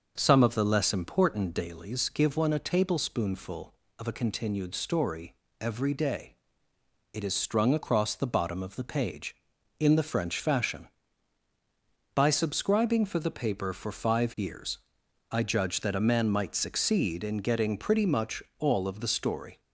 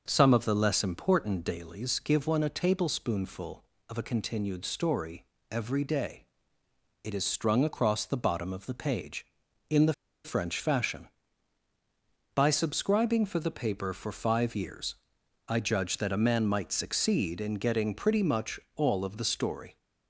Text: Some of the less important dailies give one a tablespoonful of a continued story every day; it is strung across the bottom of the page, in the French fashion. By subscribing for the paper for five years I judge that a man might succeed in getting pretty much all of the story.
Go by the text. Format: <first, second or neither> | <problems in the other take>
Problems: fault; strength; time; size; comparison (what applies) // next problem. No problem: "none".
first | starts louder than the rest; noticeable; until 1.0 s; 6 dB; noticeable in the first // pauses between "story" and "every"; slight; at 5.2 s; 0.26 s long; slight in the first // pauses between "the" and "French"; slight; at 9.9 s; 0.31 s long // pauses between "years" and "I"; noticeable; at 14.9 s; 0.52 s long; noticeable in the first // pauses between "much" and "all"; slight; at 18.5 s; 0.16 s long; slight in the first